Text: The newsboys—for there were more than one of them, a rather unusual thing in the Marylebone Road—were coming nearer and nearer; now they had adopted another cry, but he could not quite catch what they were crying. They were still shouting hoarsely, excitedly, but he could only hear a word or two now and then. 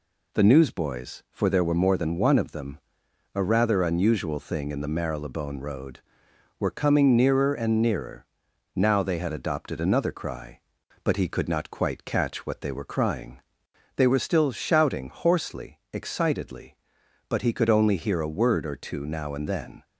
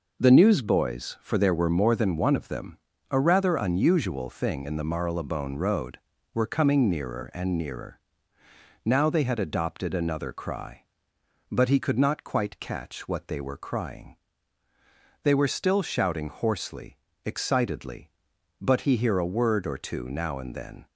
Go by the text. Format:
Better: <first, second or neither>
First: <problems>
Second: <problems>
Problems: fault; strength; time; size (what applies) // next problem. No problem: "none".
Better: first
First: none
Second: skips "could only"; at 18.9 s